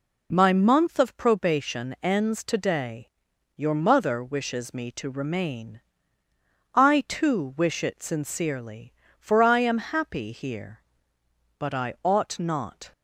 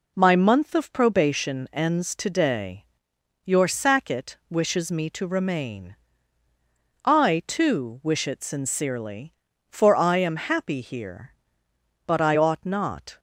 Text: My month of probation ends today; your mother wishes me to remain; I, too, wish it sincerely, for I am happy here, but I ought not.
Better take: first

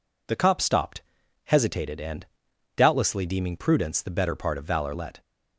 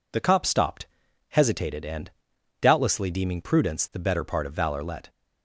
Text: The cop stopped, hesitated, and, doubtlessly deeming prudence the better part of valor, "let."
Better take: neither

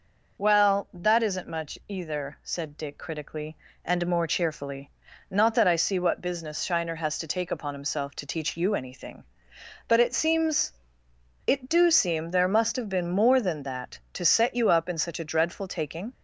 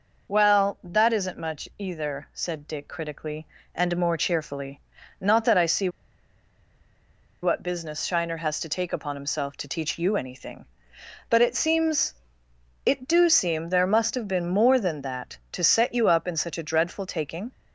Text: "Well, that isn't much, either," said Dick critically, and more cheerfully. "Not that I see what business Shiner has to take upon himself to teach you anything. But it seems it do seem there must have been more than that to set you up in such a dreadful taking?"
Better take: first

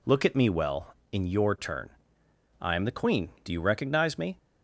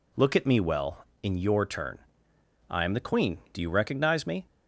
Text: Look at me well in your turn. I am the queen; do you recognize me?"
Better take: neither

